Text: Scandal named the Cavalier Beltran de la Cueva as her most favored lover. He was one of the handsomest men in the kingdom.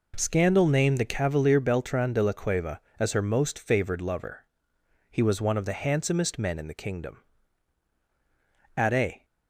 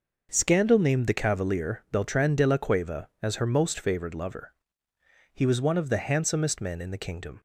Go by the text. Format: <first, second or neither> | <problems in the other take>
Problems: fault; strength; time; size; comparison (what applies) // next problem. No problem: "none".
second | goes on to say "At a"; slight; from 8.7 s on; 0.48 s long